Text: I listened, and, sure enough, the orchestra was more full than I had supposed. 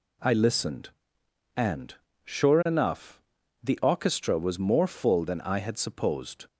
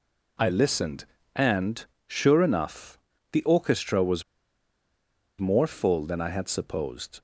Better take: first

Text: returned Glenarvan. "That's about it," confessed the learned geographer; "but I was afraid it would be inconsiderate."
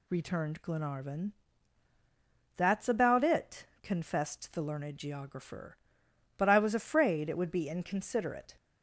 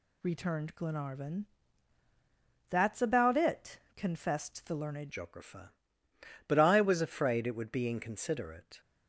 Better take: first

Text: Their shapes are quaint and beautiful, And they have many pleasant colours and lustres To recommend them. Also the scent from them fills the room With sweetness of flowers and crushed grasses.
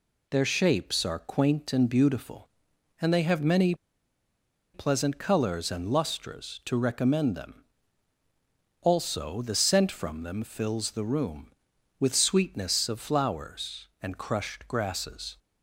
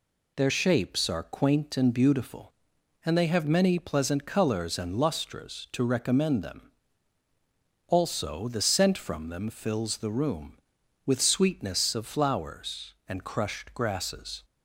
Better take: second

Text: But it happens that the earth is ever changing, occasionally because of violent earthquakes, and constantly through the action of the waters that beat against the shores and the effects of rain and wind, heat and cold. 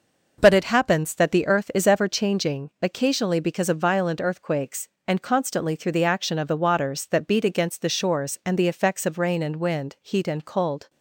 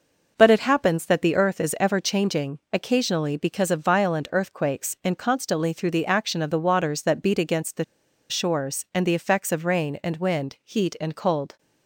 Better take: first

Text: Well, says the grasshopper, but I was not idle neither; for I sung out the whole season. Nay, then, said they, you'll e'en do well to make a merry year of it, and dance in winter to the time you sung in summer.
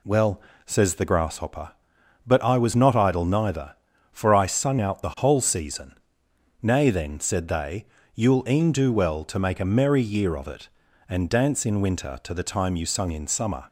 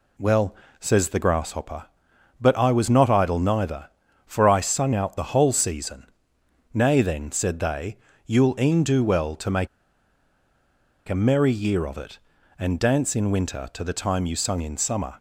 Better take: first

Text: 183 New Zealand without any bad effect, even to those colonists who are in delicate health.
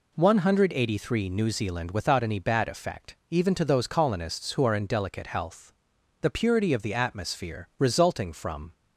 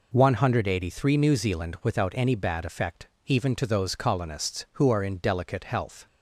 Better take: second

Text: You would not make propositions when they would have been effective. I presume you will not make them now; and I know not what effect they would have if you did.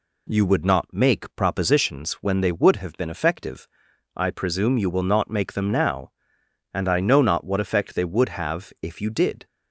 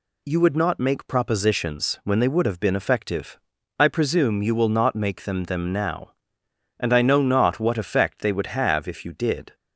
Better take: first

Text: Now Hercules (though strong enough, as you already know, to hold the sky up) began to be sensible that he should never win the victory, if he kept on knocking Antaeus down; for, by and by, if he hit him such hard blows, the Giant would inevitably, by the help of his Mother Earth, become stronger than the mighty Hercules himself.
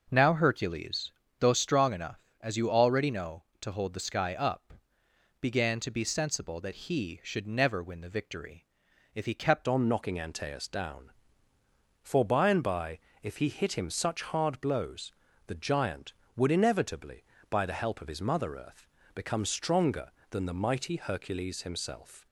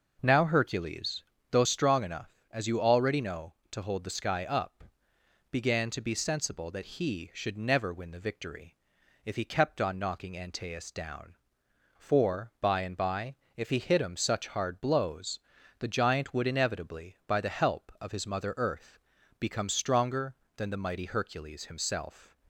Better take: second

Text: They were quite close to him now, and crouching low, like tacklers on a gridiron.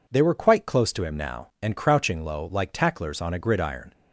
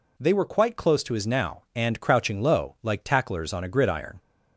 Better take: first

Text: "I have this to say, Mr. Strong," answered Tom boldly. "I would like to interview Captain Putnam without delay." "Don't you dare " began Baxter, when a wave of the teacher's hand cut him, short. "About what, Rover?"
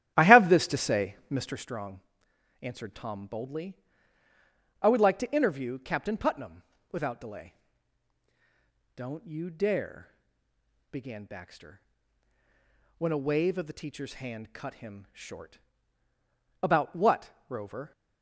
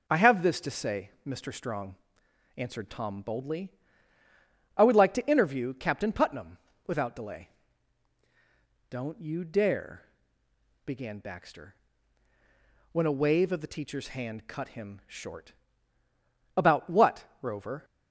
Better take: second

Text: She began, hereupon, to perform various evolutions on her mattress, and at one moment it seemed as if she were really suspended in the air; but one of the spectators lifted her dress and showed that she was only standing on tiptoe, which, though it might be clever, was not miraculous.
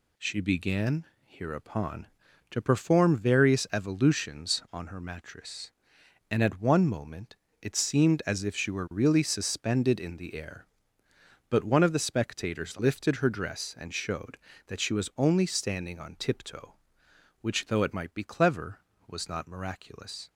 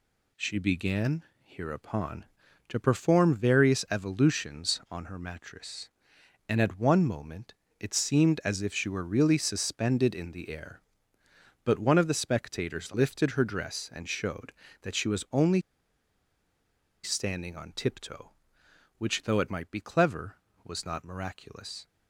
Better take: first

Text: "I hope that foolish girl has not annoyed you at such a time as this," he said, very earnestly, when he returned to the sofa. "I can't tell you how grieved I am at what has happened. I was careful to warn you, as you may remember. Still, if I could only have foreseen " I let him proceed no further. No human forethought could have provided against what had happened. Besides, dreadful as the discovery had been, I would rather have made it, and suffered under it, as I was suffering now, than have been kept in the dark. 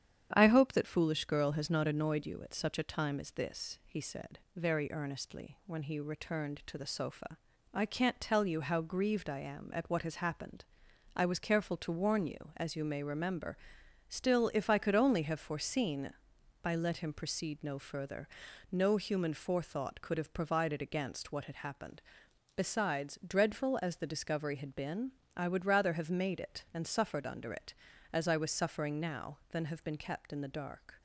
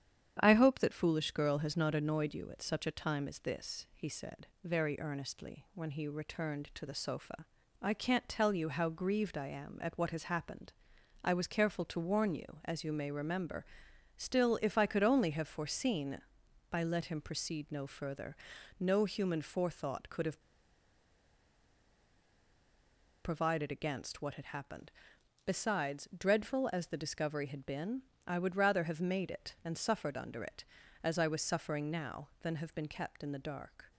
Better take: first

